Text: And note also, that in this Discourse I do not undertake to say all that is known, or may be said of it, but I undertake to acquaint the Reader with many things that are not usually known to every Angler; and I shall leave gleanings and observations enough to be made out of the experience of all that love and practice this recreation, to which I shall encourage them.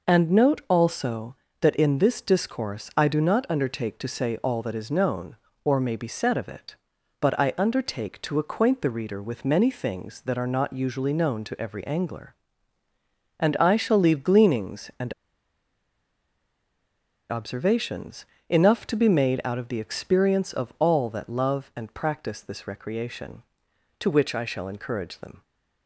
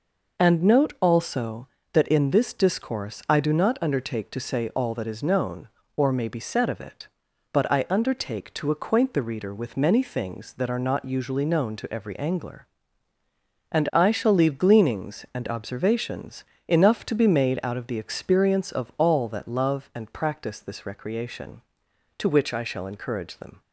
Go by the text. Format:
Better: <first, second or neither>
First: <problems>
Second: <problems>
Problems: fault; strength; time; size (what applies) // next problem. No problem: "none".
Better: second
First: pauses between "and" and "observations"; strong; at 15.1 s; 2.1 s long // pauses between "observations" and "enough"; slight; at 18.2 s; 0.24 s long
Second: pauses between "observations" and "enough"; slight; at 16.4 s; 0.24 s long